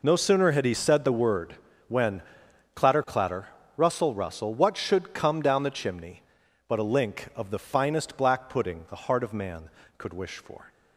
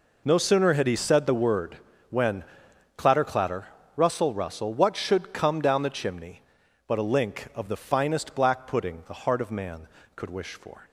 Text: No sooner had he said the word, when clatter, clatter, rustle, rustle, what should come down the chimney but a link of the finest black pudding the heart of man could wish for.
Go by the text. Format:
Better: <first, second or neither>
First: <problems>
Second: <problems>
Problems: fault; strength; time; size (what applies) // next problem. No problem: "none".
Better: neither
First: pauses between "when" and "clatter"; noticeable; at 2.2 s; 0.52 s long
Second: pauses between "when" and "clatter"; noticeable; at 2.4 s; 0.52 s long